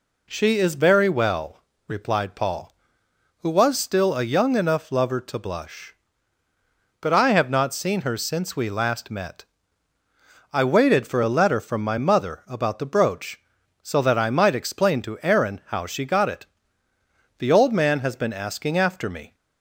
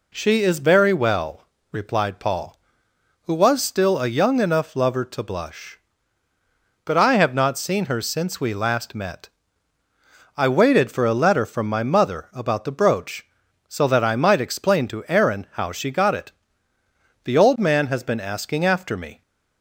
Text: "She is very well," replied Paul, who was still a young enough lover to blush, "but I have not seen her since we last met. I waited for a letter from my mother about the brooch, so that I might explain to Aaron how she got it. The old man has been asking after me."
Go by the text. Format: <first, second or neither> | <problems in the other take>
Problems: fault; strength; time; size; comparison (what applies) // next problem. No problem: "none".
neither | none